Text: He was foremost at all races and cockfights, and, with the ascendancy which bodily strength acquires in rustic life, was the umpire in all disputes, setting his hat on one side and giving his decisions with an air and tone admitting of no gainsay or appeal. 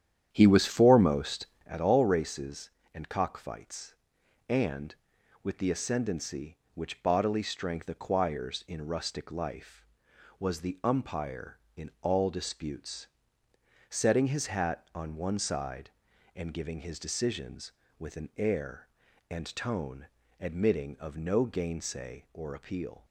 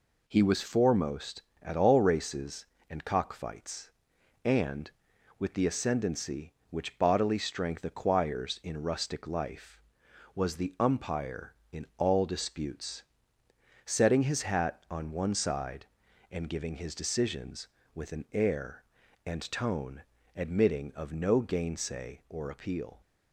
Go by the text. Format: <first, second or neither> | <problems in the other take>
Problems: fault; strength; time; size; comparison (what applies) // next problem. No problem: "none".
second | starts louder than the rest; strong; until 1.7 s; 9.5 dB // pauses between "tone" and "admitting"; slight; at 20.0 s; 0.32 s long; slight in the second